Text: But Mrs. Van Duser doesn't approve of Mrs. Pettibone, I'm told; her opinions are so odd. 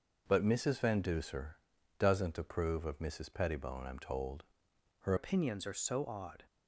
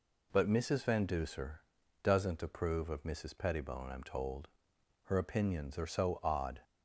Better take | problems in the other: second | pauses between "Duser" and "doesn't"; at 1.5 s; 0.44 s long; also in the second // changes voice at "opinions"; from 5.1 s on; 1.3 s long

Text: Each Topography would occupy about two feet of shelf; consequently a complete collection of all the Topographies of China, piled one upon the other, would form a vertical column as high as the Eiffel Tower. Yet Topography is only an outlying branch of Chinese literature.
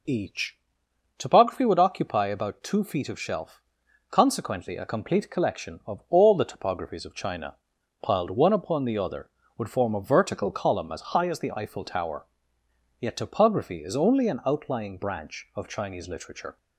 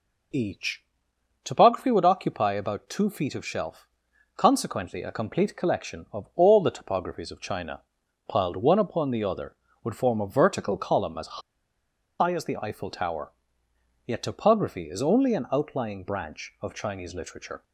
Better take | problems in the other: first | pauses between "Each" and "Topography"; noticeable; at 0.8 s; 0.62 s long; noticeable in the first // pauses between "as" and "high"; noticeable; at 11.3 s; 0.80 s long

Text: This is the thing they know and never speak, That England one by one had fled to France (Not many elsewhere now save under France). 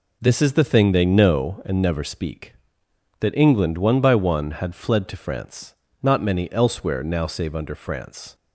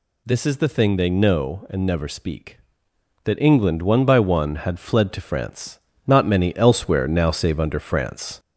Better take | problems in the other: first | gets louder; slight; throughout; 2 dB

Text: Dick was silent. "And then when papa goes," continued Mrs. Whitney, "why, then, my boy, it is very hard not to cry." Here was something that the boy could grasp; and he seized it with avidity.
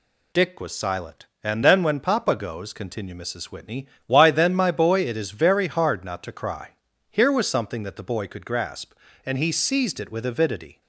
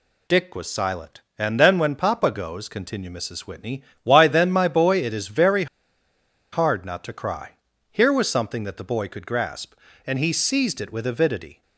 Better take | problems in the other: first | pauses between "very" and "hard"; noticeable; at 5.6 s; 0.87 s long

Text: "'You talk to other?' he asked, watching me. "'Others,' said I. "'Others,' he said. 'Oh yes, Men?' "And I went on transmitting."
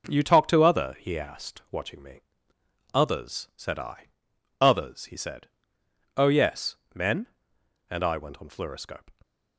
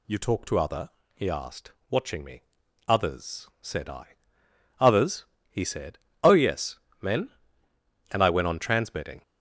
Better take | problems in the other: second | says "fluoroscope" for "transmitting"; at 8.4 s

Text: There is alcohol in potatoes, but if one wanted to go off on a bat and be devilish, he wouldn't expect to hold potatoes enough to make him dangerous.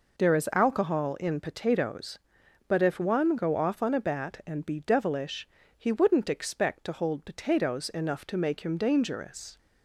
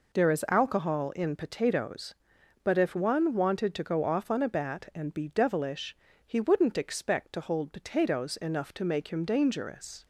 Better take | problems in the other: second | skips "wanted to"; at 3.3 s

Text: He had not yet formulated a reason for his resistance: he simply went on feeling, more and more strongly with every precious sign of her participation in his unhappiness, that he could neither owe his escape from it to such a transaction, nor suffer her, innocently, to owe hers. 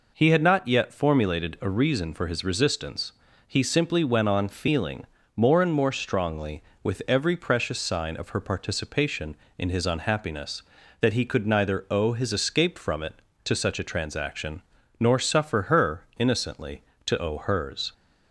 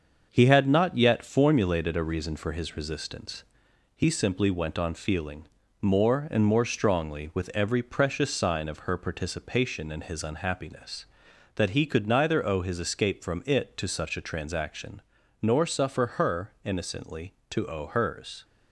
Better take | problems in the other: first | gets quieter; noticeable; throughout; 5 dB

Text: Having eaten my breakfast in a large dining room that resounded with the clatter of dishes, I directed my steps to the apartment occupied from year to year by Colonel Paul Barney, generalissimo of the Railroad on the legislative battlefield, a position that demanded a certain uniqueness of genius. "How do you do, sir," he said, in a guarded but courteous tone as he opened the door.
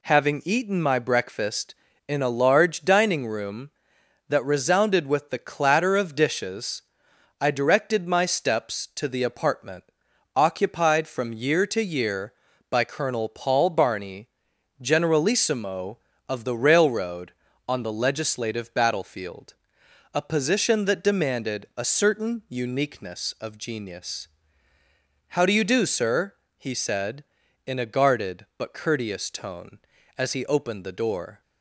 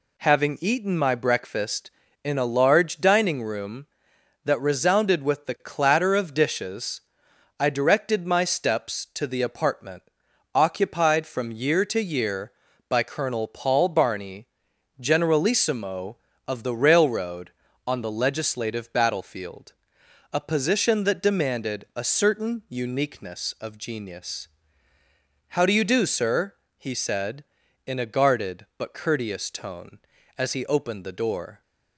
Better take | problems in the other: neither | pauses between "apartment" and "occupied"; noticeable; the same in both

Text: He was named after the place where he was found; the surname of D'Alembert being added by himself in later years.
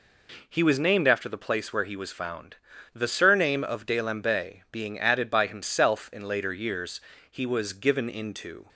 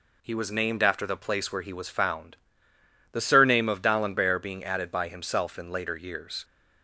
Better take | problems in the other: second | goes on to say "He was given into"; from 7.3 s on; 1.3 s long

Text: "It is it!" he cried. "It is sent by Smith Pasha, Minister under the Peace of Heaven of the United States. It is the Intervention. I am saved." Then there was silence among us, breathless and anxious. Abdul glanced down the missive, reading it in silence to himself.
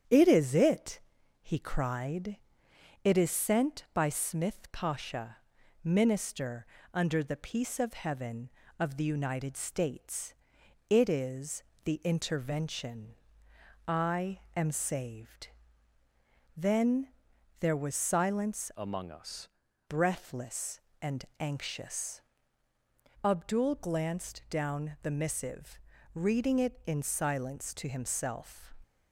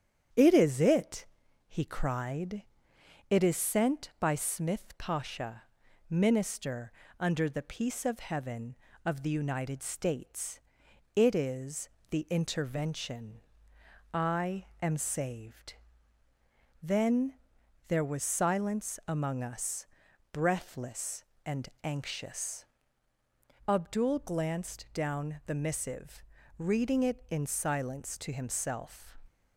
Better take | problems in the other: second | starts louder than the rest; strong; until 1.5 s; 9 dB; strong in the second // pauses between "Minister" and "under"; slight; at 6.6 s; 0.28 s long; slight in the second // pauses between "is" and "the"; slight; at 11.6 s; 0.22 s long; slight in the second // pauses between "Then" and "there"; noticeable; at 17.1 s; 0.46 s long; noticeable in the second // changes voice from "among" to "us"; from 18.7 to 19.4 s; 0.7 s long // pauses between "and" and "anxious"; slight; at 21.2 s; 0.16 s long; slight in the second

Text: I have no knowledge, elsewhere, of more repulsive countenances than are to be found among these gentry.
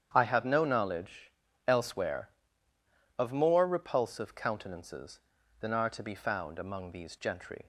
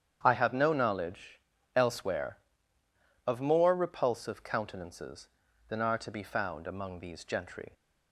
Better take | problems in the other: neither | starts louder than the rest; strong; the same in both

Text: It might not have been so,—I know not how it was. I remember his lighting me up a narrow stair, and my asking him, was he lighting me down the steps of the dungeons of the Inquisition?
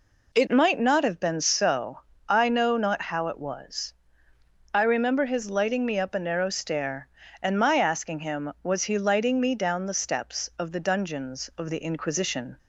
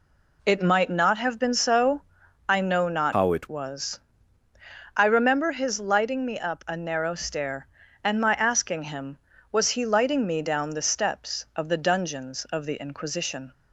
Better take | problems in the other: first | changes voice from "how" to "it"; from 3.1 to 3.4 s; 0.3 s long

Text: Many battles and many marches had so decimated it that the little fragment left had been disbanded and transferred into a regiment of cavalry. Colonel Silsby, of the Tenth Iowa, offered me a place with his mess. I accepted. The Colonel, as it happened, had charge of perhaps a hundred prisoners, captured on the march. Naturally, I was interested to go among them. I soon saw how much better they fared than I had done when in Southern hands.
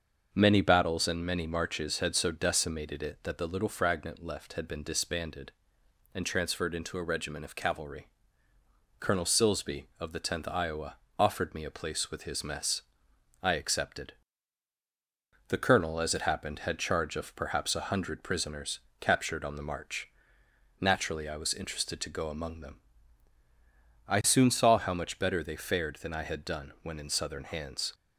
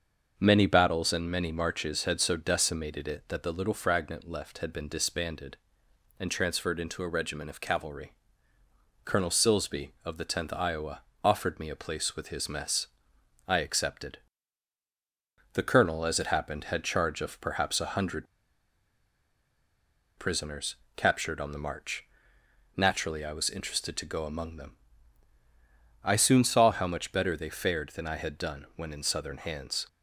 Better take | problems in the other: first | starts louder than the rest; until 1.3 s; 6.5 dB; also in the first // pauses between "hundred" and "prisoners"; strong; at 18.2 s; 1.9 s long

